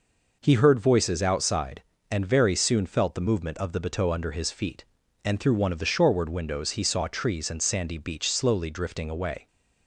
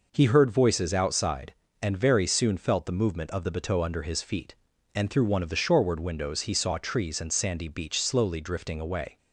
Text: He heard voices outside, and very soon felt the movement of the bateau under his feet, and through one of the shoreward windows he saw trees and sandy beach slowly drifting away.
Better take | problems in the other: neither | none

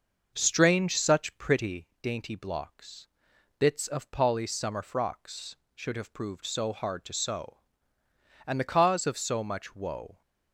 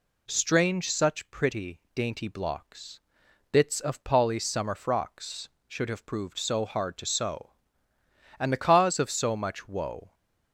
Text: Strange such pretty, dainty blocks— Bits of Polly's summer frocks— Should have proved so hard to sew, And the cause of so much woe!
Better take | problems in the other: second | starts louder than the rest; noticeable; until 1.9 s; 6 dB

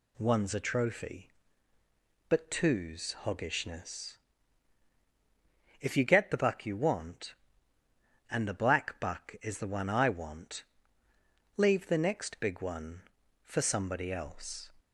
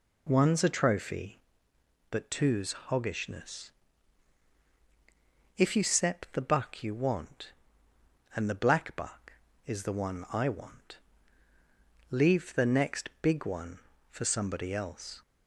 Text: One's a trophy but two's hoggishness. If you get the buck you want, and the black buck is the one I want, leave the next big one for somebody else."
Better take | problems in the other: first | says "sep" for "get"; at 5.8 s

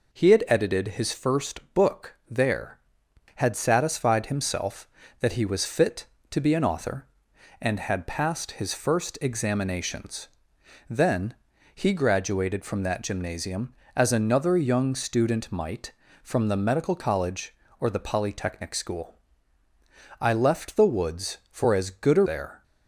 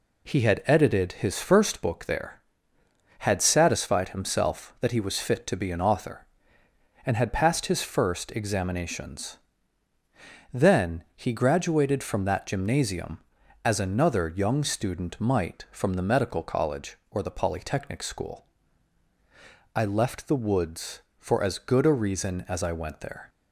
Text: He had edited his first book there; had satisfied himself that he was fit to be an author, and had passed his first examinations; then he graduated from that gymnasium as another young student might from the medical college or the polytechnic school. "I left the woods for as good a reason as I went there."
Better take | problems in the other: second | pauses between "then" and "he"; at 11.3 s; 0.40 s long // skips "reason as I went"; at 22.2 s

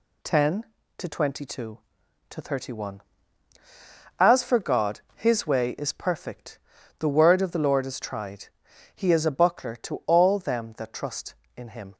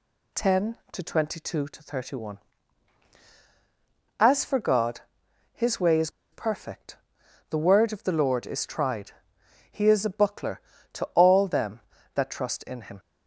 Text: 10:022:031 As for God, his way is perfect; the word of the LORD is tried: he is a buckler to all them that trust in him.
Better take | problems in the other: first | pauses between "is" and "perfect"; slight; at 6.0 s; 0.23 s long

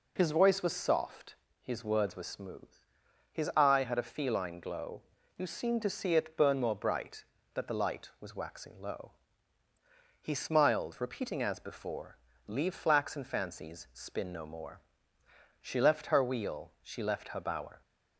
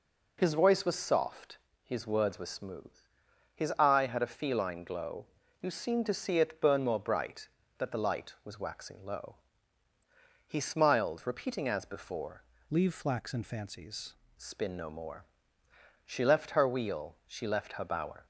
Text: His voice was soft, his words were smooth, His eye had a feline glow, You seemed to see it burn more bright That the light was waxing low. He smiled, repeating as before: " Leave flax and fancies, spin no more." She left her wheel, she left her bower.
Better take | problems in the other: first | changes voice from "Leave" to "fancies"; from 12.7 to 14.1 s; 1.4 s long

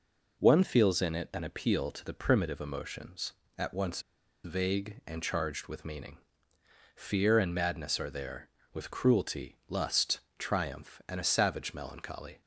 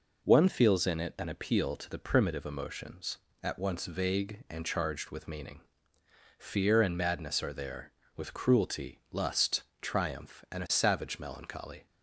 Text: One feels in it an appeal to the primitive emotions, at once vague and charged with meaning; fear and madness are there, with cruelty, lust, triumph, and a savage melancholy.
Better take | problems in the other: second | pauses between "once" and "vague"; at 4.0 s; 0.43 s long

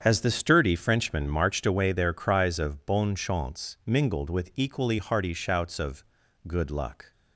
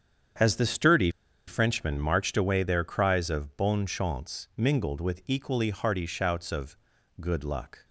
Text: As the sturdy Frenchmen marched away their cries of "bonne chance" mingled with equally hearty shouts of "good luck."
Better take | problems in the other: first | starts louder than the rest; strong; until 1.7 s; 8 dB; strong in the first // pauses between "sturdy" and "Frenchmen"; at 1.0 s; 0.38 s long // pauses between "of" and "good"; at 6.7 s; 0.44 s long; also in the first

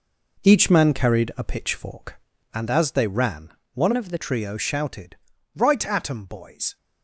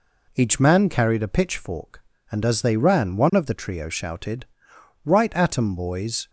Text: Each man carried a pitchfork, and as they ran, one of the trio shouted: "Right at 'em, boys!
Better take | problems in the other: second | changes voice from "of" to "the"; from 3.9 to 4.1 s; 0.2 s long

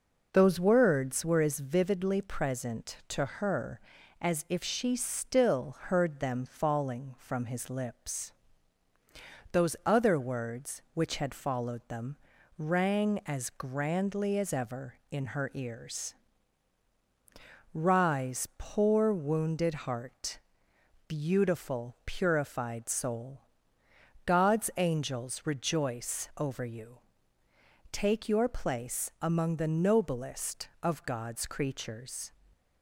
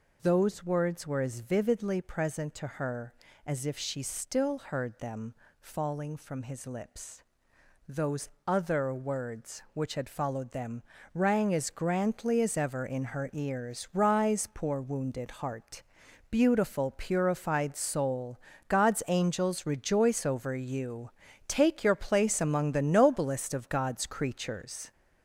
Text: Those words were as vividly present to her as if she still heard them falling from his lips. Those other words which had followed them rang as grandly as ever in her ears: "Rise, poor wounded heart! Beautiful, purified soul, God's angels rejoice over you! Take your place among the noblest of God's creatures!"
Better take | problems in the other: first | gets louder; noticeable; throughout; 5 dB // pauses between "them" and "falling"; slight; at 5.3 s; 0.28 s long // pauses between "Those" and "other"; slight; at 8.2 s; 0.18 s long // pauses between "them" and "rang"; slight; at 10.8 s; 0.32 s long; also in the first

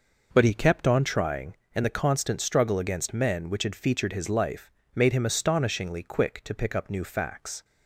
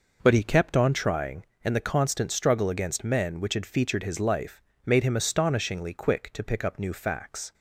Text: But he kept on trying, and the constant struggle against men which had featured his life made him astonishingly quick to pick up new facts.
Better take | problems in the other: neither | pauses between "life" and "made"; slight; the same in both

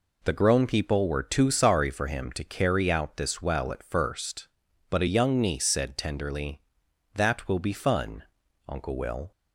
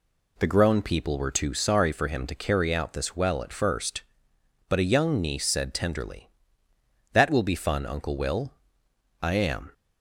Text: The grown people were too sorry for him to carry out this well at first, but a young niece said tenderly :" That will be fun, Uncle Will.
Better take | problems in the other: first | goes on to say "I am"; from 9.2 s on; 0.52 s long

